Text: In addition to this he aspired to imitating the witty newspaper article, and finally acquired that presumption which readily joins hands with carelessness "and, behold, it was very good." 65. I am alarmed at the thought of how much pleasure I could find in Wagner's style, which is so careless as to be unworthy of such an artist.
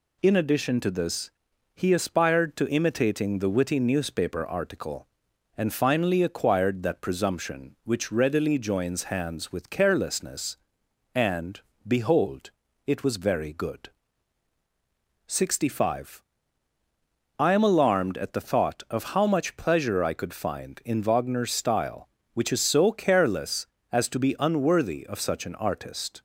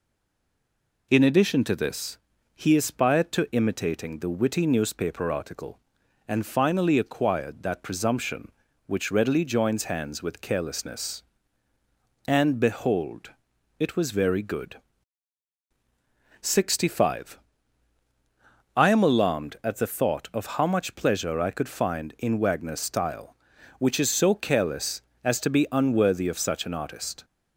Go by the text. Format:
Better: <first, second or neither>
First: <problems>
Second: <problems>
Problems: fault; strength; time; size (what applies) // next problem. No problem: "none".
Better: first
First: pauses between "this" and "he"; at 1.3 s; 0.44 s long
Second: stays silent before the first word; until 1.1 s; 1.1 s long // pauses between "this" and "he"; slight; at 2.1 s; 0.36 s long